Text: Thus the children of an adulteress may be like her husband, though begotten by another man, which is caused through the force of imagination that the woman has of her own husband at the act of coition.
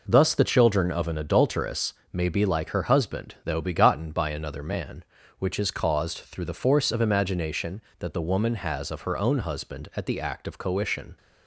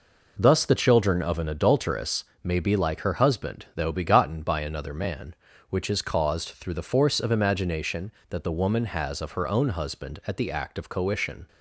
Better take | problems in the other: neither | pauses between "adulteress" and "may"; slight; the same in both

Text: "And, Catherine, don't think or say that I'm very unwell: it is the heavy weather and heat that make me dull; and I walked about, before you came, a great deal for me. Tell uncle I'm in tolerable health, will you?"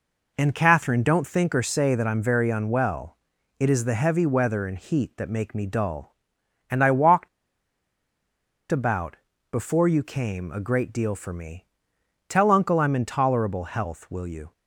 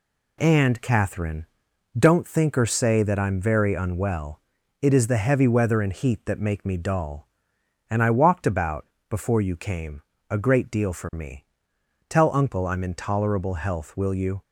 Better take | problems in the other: second | pauses between "walked" and "about"; strong; at 7.2 s; 1.4 s long

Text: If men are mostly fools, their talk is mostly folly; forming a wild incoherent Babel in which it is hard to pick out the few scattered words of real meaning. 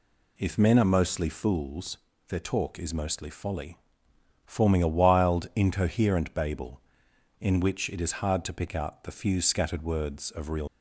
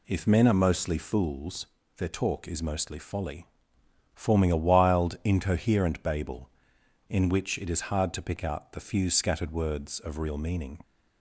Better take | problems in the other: second | stops before "meaning"; at 10.6 s

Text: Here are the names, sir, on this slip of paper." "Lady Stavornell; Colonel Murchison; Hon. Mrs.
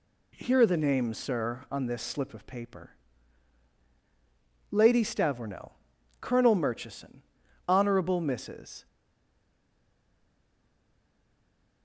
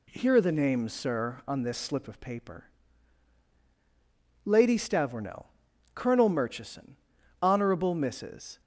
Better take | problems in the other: second | stays silent after the last word; strong; from 8.8 s on; 3.0 s long

